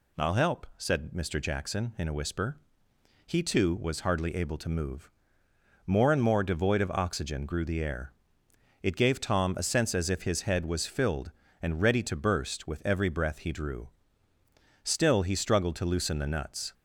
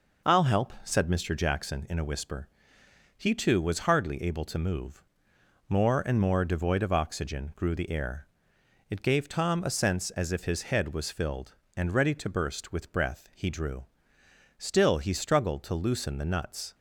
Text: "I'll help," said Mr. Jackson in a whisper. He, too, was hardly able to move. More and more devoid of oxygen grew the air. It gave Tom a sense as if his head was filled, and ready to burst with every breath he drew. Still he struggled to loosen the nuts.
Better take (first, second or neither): first